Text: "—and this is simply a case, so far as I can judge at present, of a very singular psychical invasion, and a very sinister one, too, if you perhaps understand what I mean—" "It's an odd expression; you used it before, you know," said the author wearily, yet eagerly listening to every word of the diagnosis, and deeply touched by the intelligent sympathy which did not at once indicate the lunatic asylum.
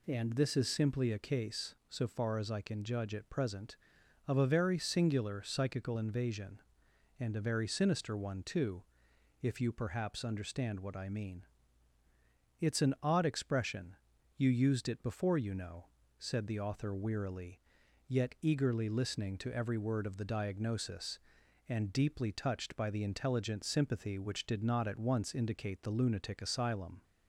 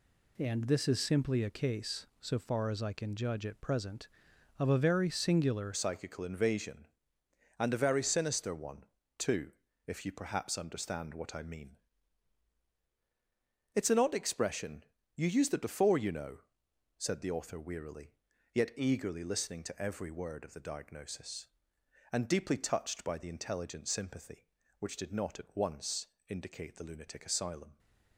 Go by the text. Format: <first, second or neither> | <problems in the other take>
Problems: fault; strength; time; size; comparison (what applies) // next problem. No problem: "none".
first | changes voice at "psychical"; from 5.7 s on; 22.0 s long // pauses between "once" and "indicate"; slight; at 26.0 s; 0.20 s long